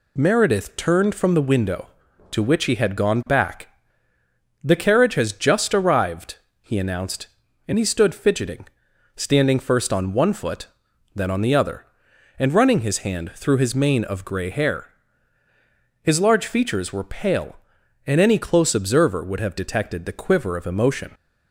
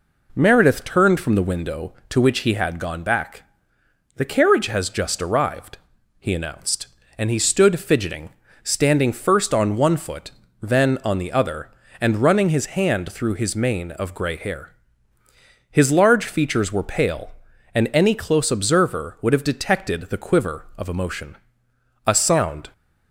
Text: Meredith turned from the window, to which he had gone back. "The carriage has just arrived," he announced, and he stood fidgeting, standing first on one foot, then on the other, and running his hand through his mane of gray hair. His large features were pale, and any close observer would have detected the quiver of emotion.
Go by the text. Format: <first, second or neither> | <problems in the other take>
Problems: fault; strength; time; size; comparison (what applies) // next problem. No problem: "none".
first | goes on to say "A sound"; noticeable; from 22.0 s on; 0.64 s long